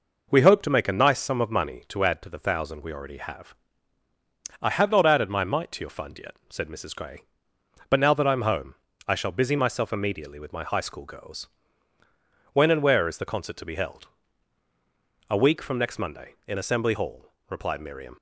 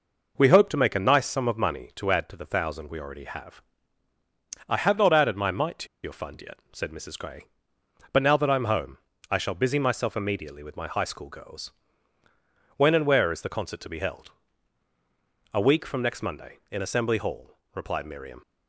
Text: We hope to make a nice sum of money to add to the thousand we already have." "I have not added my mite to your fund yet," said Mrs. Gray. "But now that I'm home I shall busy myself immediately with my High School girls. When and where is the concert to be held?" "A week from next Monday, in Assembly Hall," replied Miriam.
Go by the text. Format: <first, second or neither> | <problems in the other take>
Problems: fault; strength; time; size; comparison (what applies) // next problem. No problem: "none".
first | pauses between "to" and "your"; slight; at 5.8 s; 0.16 s long // pauses between "home" and "I"; slight; at 8.9 s; 0.32 s long; slight in the first